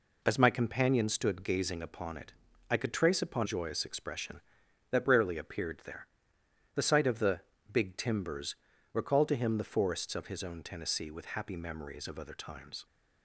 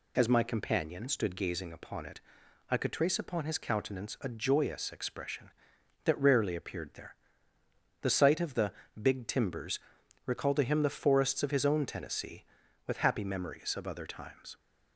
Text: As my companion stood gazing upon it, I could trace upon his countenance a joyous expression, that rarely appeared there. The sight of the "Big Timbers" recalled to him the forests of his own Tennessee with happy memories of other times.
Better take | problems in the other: second | skips "his countenance a"; at 3.4 s // pauses between "the" and "Big"; slight; at 7.4 s; 0.30 s long; slight in the second // pauses between "Timbers" and "recalled"; at 8.5 s; 0.38 s long; also in the second

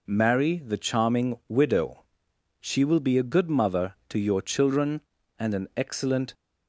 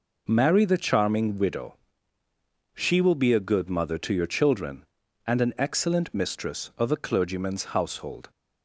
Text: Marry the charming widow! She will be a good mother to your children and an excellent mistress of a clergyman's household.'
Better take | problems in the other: second | stops before "mistress of a clergyman's household"; at 6.3 s

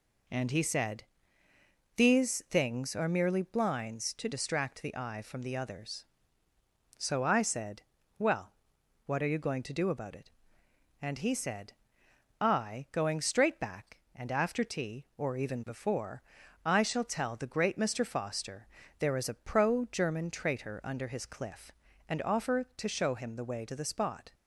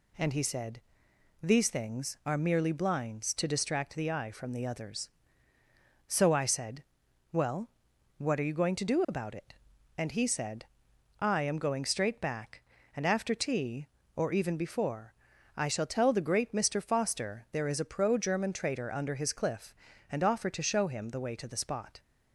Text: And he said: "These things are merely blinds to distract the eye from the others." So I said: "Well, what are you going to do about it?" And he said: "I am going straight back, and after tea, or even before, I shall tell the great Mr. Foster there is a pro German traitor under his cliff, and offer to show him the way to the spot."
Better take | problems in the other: second | skips "am"; at 12.8 s // pauses between "Foster" and "there"; slight; at 18.6 s; 0.32 s long

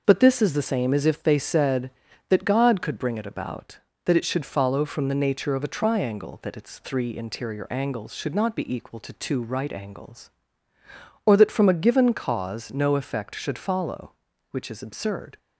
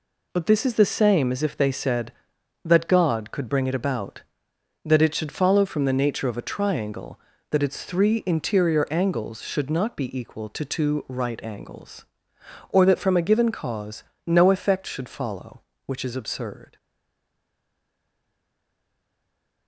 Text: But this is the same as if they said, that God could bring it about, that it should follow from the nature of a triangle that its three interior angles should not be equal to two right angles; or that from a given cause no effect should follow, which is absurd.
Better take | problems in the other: first | pauses between "cause" and "no"; slight; at 14.0 s; 0.20 s long // stays silent after the last word; strong; from 16.7 s on; 2.9 s long

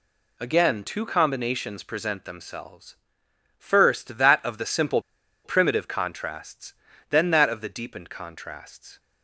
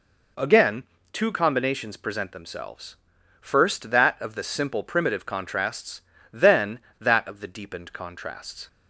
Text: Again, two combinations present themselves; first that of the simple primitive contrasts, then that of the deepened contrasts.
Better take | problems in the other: second | pauses between "simple" and "primitive"; at 4.9 s; 0.45 s long

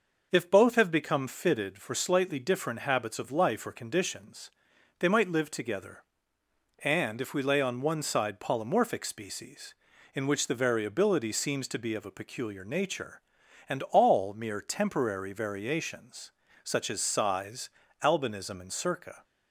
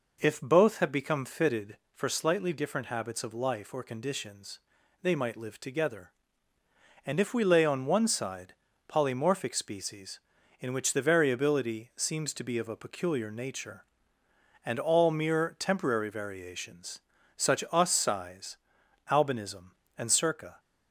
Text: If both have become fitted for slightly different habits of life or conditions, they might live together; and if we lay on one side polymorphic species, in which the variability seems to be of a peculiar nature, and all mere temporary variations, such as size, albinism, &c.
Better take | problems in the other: first | pauses between "side" and "polymorphic"; slight; at 8.5 s; 0.36 s long // says "us" for "as"; at 17.7 s

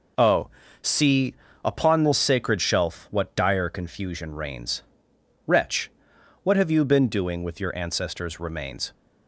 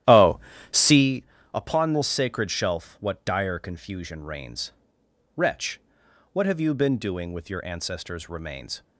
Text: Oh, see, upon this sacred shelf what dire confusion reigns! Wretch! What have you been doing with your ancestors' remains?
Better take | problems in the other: first | starts louder than the rest; strong; until 1.1 s; 12.5 dB

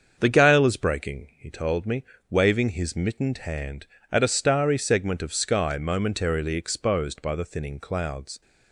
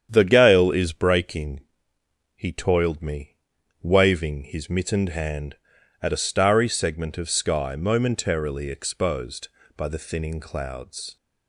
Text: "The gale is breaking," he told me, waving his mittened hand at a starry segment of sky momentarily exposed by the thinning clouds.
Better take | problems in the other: first | starts louder than the rest; strong; until 1.1 s; 8.5 dB; also in the first // says "toiled" for "told"; at 2.4 s

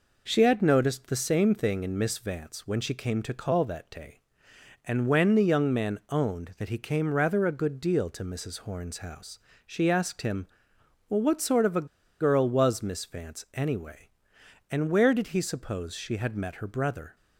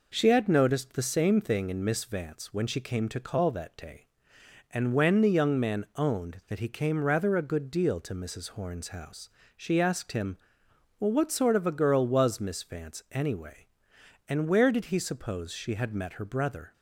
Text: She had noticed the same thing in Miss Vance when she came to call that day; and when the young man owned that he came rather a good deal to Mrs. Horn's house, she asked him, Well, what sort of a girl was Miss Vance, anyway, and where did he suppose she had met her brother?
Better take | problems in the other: second | pauses between "a" and "girl"; slight; at 11.8 s; 0.34 s long

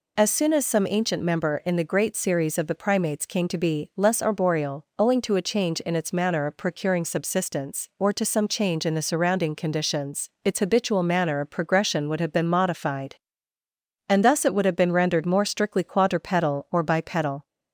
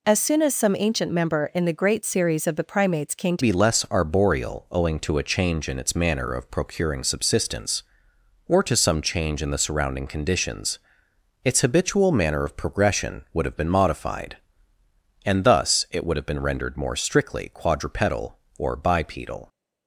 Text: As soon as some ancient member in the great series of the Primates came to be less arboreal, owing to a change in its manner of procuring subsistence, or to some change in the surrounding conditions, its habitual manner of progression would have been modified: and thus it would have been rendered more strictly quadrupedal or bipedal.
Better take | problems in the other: first | changes voice at "be"; from 3.4 s on; 16.0 s long

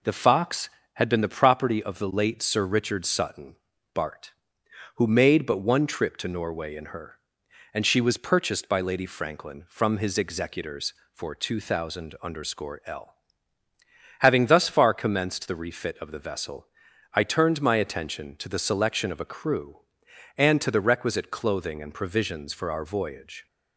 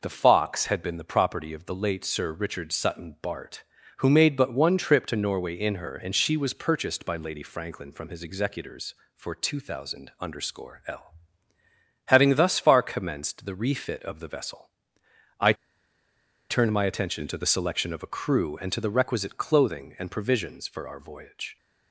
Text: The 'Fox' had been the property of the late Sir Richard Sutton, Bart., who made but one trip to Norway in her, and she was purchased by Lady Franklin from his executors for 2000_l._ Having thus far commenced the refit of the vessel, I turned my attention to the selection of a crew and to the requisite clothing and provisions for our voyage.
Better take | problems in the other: first | pauses between "I" and "turned"; noticeable; at 15.5 s; 0.95 s long

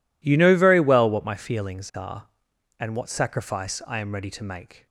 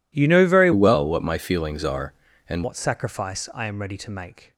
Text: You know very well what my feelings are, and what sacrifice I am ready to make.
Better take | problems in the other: first | changes voice from "well" to "and"; from 0.7 to 2.6 s; 1.9 s long

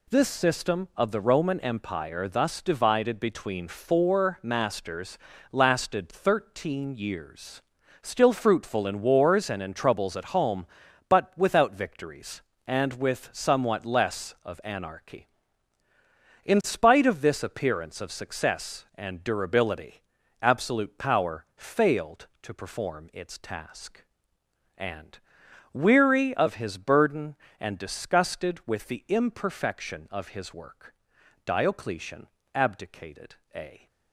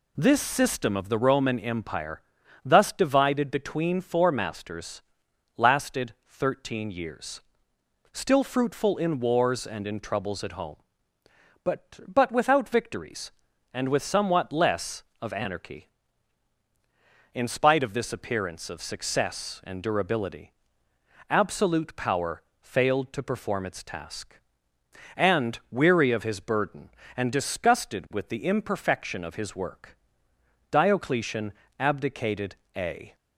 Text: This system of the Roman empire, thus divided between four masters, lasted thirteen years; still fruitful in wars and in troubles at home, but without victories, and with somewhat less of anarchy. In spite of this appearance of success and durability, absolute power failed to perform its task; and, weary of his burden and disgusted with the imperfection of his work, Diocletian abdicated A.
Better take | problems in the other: first | says "but" twice; at 12.0 s // pauses between "power" and "failed"; slight; at 22.4 s; 0.20 s long // pauses between "Diocletian" and "abdicated"; slight; at 31.5 s; 0.26 s long; slight in the first // pauses between "abdicated" and "A"; slight; at 32.5 s; 0.20 s long; slight in the first

